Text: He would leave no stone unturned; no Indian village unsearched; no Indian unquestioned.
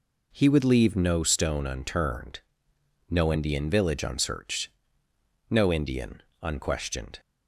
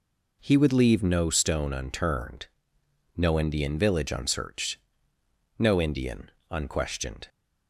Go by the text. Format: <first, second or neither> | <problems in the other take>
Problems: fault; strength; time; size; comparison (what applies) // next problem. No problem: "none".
neither | pauses between "Indian" and "unquestioned"; slight; the same in both